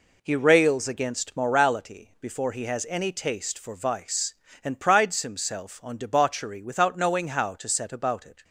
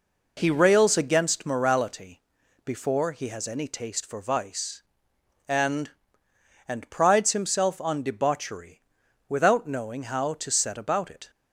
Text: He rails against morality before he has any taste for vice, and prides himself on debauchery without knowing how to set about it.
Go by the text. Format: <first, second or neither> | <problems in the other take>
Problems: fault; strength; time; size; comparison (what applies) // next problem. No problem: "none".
first | pauses between "morality" and "before"; at 2.1 s; 0.44 s long // says "and" twice; at 6.6 s // pauses between "debauchery" and "without"; noticeable; at 8.7 s; 0.48 s long